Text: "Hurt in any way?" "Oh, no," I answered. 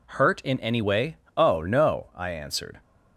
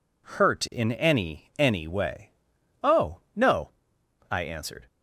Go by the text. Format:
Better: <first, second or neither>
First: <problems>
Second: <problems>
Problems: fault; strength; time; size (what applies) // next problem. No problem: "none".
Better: first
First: none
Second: says "any" twice; at 1.5 s